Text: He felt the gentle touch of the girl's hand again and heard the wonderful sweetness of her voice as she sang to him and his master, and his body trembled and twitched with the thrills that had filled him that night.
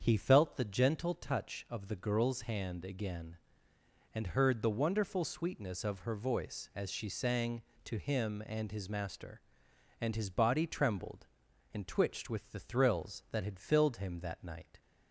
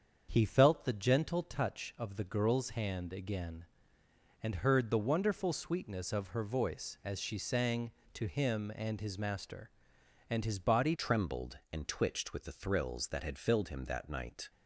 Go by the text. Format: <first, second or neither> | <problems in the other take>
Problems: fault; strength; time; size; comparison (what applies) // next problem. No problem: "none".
first | starts louder than the rest; strong; until 1.3 s; 7 dB; strong in the first // changes voice at "trembled"; from 10.9 s on; 3.5 s long